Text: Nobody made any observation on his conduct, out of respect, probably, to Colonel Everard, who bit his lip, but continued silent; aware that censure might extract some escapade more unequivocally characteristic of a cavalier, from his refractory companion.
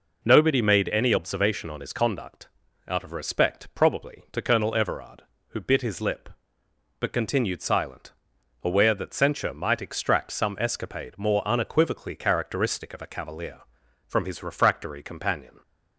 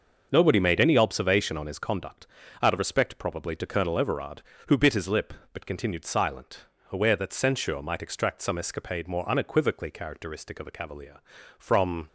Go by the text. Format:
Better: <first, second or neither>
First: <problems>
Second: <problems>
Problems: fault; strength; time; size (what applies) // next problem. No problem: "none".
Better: first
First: none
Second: starts louder than the rest; noticeable; until 1.3 s; 6 dB // stops before "his refractory companion"; at 12.0 s